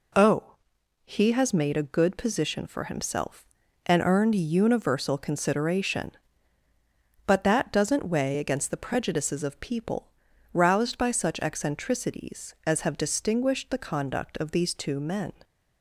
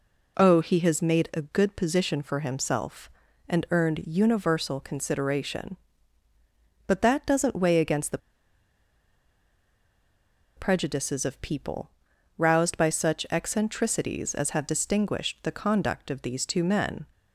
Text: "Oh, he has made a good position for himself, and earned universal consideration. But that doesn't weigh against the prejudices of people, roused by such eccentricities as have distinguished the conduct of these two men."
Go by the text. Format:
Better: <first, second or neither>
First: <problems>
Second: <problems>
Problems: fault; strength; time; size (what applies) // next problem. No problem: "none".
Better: first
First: none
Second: pauses between "the" and "prejudices"; strong; at 8.1 s; 2.3 s long